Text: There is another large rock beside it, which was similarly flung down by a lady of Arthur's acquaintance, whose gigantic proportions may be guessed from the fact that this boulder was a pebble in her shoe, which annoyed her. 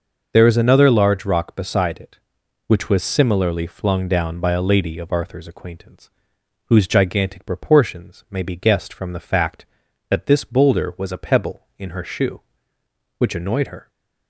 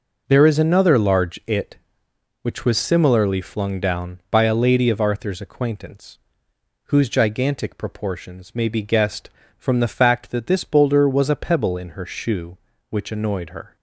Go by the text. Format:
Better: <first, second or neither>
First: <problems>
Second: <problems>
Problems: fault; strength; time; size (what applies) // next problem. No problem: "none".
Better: first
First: none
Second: skips "rock beside"; at 1.4 s